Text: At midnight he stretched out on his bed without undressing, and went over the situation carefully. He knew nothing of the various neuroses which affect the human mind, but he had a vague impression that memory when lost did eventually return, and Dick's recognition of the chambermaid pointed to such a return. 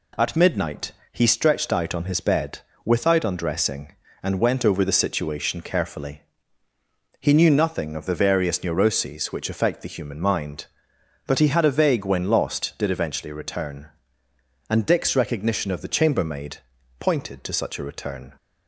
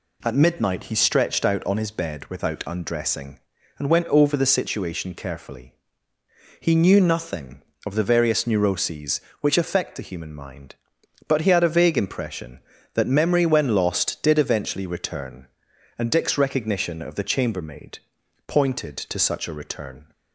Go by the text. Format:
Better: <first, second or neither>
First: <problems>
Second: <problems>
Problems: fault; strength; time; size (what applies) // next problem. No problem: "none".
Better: second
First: pauses between "midnight" and "he"; slight; at 0.9 s; 0.20 s long // pauses between "bed" and "without"; slight; at 2.6 s; 0.24 s long // skips "impression that memory"; at 12.0 s // pauses between "chambermaid" and "pointed"; at 16.5 s; 0.42 s long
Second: pauses between "chambermaid" and "pointed"; noticeable; at 17.9 s; 0.48 s long